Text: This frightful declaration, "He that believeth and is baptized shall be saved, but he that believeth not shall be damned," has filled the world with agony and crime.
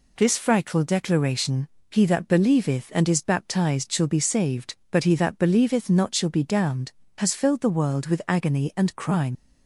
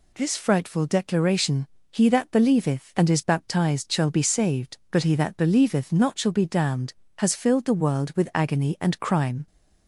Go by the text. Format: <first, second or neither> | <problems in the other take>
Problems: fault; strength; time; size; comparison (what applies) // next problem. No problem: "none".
second | leaves "crime" unfinished; at 9.3 s; 90 ms